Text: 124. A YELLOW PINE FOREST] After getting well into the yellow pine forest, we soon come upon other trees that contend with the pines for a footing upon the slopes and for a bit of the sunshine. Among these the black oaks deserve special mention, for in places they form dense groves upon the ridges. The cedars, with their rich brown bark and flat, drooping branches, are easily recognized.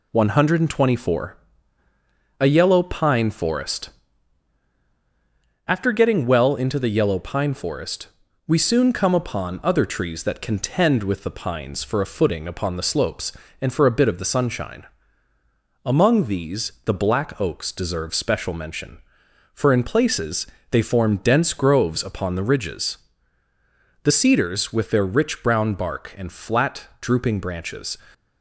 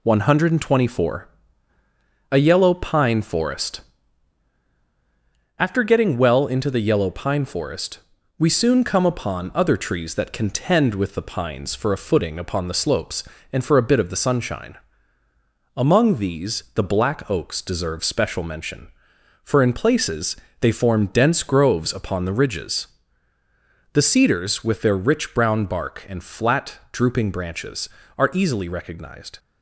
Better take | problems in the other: second | pauses between "FOREST" and "After"; strong; at 3.9 s; 1.7 s long; strong in the second // pauses between "places" and "they"; slight; at 20.4 s; 0.24 s long; slight in the second // stops before "are easily recognized"; at 28.1 s

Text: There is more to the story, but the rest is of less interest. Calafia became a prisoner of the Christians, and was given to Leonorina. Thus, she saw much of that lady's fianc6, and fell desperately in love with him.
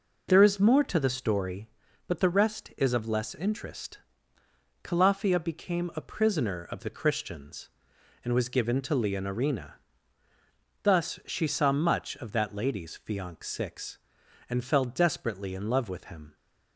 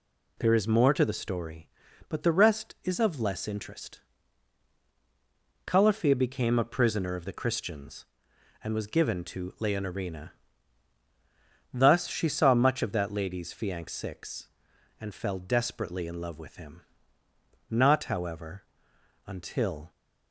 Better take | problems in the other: first | goes on to say "Not however until"; strong; from 17.6 s on; 2.2 s long

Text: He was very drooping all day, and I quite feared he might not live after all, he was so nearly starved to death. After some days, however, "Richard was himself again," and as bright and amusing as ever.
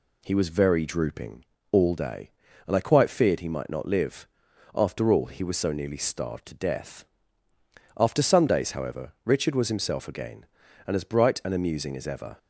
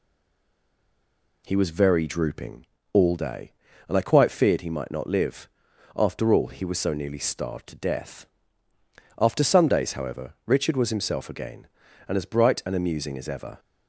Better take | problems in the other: first | stays silent before the first word; noticeable; until 1.4 s; 1.4 s long // pauses between "drooping" and "all"; slight; at 2.6 s; 0.28 s long; slight in the first // pauses between "live" and "after"; noticeable; at 5.4 s; 0.46 s long; noticeable in the first

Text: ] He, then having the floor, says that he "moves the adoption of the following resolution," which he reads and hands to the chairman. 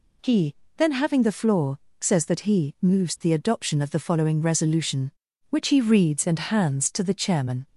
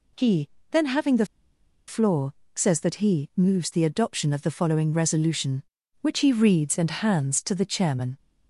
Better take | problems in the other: first | pauses between "the" and "floor"; noticeable; at 1.2 s; 0.62 s long

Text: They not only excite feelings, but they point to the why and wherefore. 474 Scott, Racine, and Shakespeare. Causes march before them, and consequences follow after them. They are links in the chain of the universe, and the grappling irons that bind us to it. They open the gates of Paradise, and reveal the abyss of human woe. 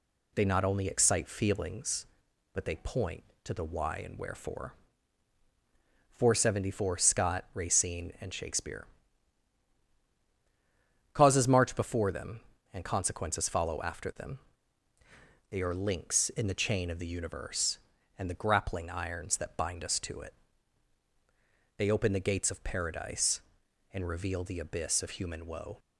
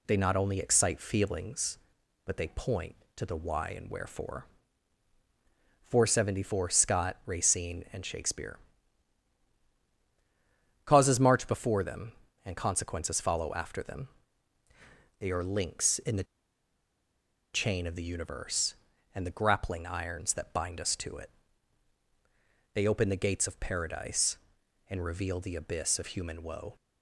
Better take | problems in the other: first | pauses between "the" and "chain"; strong; at 16.2 s; 1.2 s long

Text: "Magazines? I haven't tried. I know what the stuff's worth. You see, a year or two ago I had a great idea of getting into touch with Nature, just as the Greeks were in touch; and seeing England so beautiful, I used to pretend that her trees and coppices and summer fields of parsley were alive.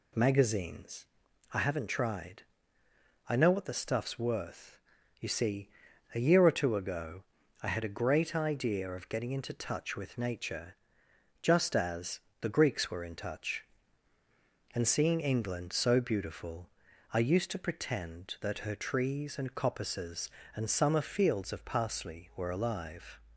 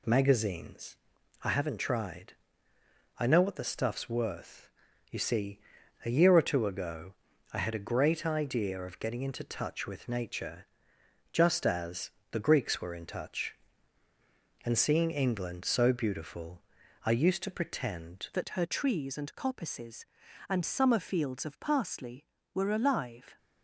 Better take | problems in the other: first | pauses between "ago" and "I"; at 7.1 s; 0.40 s long; also in the first // pauses between "as" and "the"; slight; at 12.1 s; 0.22 s long; slight in the first // changes voice at "that"; from 18.3 s on; 5.0 s long

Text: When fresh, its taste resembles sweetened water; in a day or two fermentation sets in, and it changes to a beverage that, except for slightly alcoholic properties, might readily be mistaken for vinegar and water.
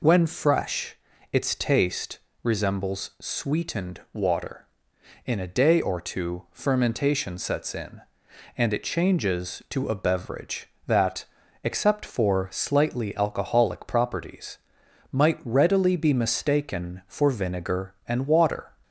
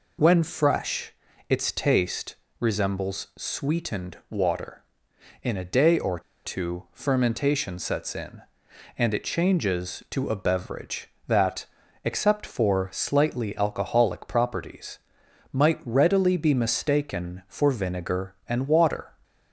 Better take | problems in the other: first | pauses between "taste" and "resembles"; slight; at 2.3 s; 0.24 s long; slight in the first // pauses between "or" and "two"; slight; at 6.1 s; 0.25 s long

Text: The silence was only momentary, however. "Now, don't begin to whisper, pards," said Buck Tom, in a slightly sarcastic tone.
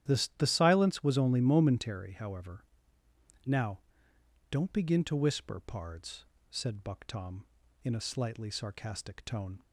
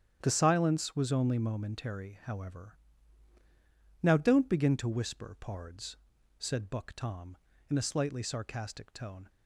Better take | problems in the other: second | starts louder than the rest; strong; until 1.1 s; 11 dB; strong in the second // says "The" twice; at 0.3 s

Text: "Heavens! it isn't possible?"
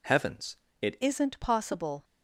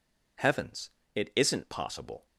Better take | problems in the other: second | changes voice at "isn't"; from 1.0 s on; 1.0 s long

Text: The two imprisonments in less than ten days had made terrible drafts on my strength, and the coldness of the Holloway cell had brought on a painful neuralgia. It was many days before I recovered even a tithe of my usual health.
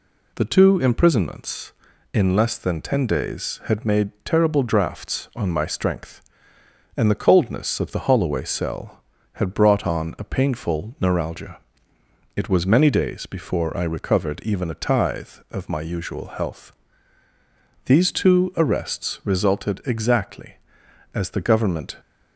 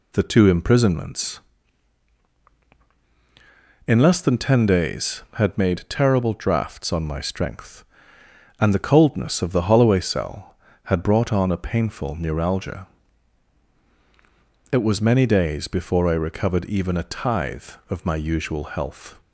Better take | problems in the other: second | goes on to say "These two arrests resulted exactly as the Government"; strong; from 17.8 s on; 4.1 s long

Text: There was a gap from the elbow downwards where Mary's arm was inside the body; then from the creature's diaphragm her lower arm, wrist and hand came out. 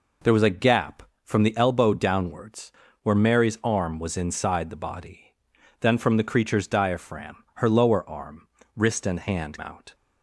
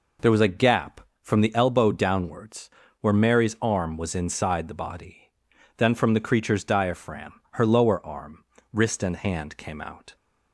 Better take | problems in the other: second | pauses between "downwards" and "where"; slight; at 2.7 s; 0.32 s long; slight in the second // skips "came"; at 9.5 s

